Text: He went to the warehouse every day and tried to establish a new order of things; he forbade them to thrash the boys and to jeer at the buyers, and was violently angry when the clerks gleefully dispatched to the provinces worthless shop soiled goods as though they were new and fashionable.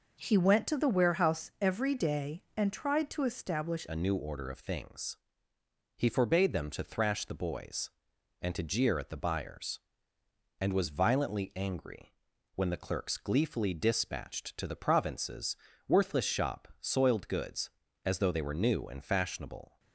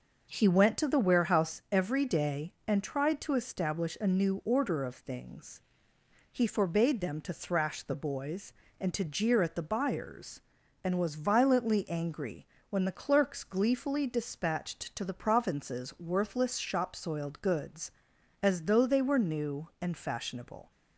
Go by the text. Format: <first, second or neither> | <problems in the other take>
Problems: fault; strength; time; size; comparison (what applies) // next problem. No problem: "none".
second | changes voice at "a"; from 3.8 s on; 15.9 s long // pauses between "angry" and "when"; at 12.1 s; 0.40 s long; slight in the second // pauses between "provinces" and "worthless"; slight; at 15.5 s; 0.32 s long